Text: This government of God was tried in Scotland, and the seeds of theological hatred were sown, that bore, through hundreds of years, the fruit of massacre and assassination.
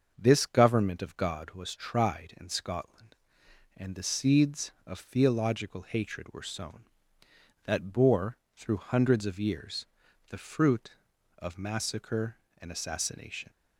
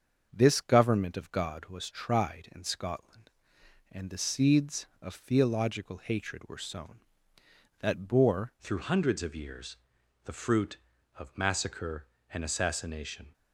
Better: first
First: starts louder than the rest; until 1.1 s; 6.5 dB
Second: starts louder than the rest; until 1.3 s; 7 dB // changes voice at "through"; from 8.6 s on; 4.7 s long

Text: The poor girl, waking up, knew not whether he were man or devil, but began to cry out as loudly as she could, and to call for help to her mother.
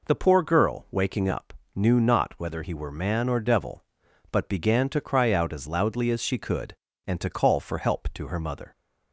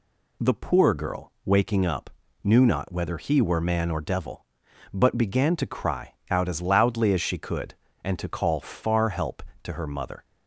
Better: first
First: none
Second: pauses between "cry" and "out"; slight; at 6.1 s; 0.18 s long // says "far" for "for"; at 8.5 s

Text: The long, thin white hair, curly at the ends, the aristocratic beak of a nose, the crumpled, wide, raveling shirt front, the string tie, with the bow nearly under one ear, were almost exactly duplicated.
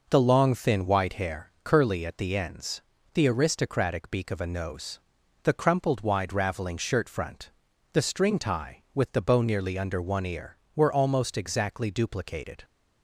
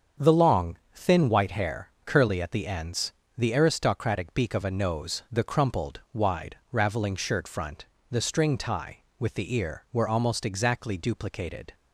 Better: first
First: none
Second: starts louder than the rest; until 1.3 s; 7 dB // skips "bow nearly under one"; at 9.5 s

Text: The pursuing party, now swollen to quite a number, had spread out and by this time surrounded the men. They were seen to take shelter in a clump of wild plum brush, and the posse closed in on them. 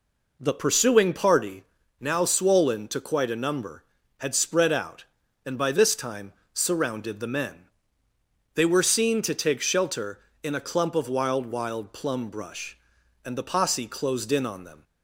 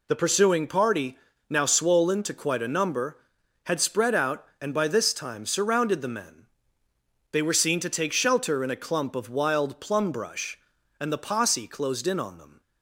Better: second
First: pauses between "time" and "surrounded"; slight; at 6.3 s; 0.20 s long // says "wild" twice; at 11.4 s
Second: none

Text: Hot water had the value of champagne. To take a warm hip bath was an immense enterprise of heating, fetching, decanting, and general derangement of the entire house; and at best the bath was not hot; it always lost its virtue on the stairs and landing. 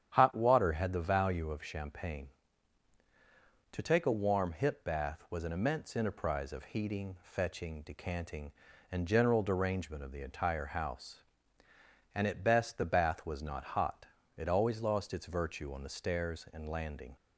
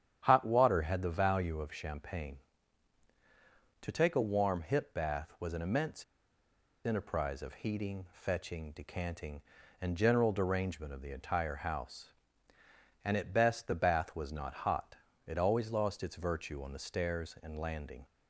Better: first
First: starts louder than the rest; strong; until 1.1 s; 9.5 dB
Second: starts louder than the rest; strong; until 1.2 s; 9 dB // pauses between "immense" and "enterprise"; noticeable; at 6.0 s; 0.80 s long

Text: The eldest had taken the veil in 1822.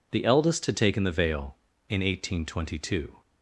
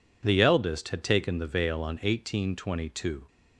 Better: first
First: none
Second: says "on" for "in"; at 1.8 s

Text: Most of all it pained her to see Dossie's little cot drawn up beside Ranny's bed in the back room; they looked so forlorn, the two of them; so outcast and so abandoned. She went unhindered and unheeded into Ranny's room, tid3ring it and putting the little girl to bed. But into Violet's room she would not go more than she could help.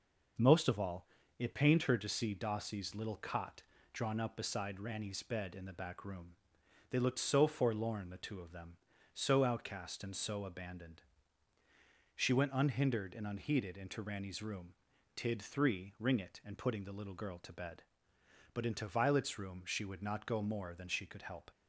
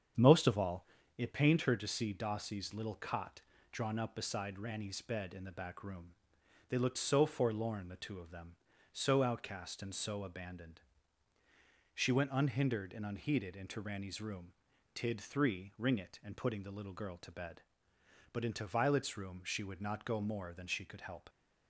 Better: first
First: pauses between "all" and "it"; slight; at 1.0 s; 0.32 s long // pauses between "cot" and "drawn"; slight; at 3.6 s; 0.30 s long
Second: starts louder than the rest; strong; until 1.2 s; 7.5 dB // pauses between "all" and "it"; slight; at 0.8 s; 0.32 s long // pauses between "cot" and "drawn"; slight; at 3.4 s; 0.30 s long

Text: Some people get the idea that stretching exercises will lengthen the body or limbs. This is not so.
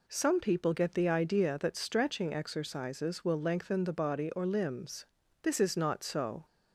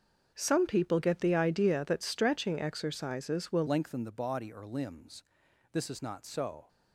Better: first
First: none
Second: starts louder than the rest; until 1.3 s; 7 dB // changes voice at "lengthen"; from 3.6 s on; 3.0 s long

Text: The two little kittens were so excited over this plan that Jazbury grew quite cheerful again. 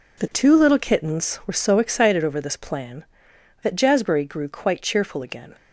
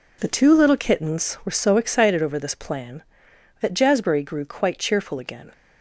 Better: neither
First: none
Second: none

